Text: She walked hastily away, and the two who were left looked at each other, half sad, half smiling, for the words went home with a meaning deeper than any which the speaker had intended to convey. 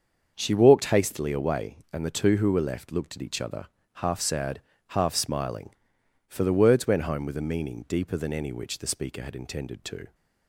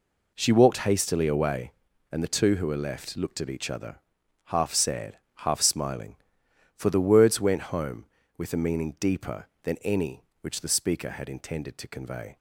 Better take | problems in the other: second | starts louder than the rest; until 1.3 s; 6.5 dB // stops before "convey"; at 10.1 s

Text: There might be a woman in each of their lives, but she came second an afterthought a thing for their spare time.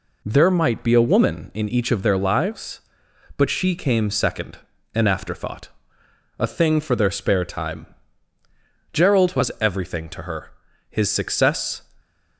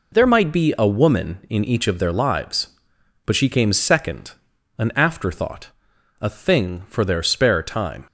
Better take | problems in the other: second | pauses between "second" and "an"; slight; at 4.5 s; 0.36 s long; noticeable in the second // pauses between "afterthought" and "a"; noticeable; at 5.6 s; 0.70 s long; noticeable in the second // goes on to say "Gerald was everything to her His success"; strong; from 8.9 s on; 2.9 s long

